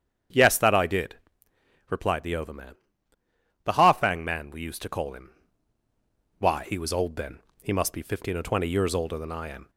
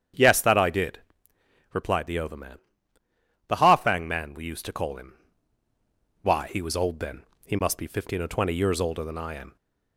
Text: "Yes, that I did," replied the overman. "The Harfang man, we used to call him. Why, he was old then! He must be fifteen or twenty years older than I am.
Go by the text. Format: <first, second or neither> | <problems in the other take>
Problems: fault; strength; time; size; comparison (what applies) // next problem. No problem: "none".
neither | starts louder than the rest; strong; the same in both